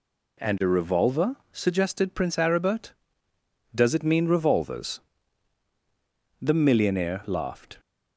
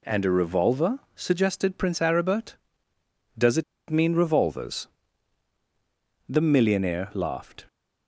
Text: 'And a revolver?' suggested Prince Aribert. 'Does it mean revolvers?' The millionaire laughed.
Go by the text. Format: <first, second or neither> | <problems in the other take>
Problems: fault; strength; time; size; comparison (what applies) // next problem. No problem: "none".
first | pauses between "it" and "mean"; slight; at 3.6 s; 0.26 s long